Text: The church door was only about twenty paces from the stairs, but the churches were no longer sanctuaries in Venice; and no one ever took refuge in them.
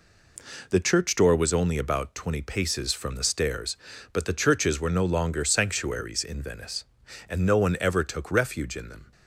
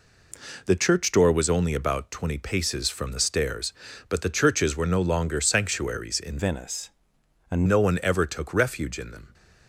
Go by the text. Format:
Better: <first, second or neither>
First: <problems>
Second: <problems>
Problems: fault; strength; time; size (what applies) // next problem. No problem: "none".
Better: first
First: none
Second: changes voice from "Venice" to "and"; from 6.3 to 7.6 s; 1.3 s long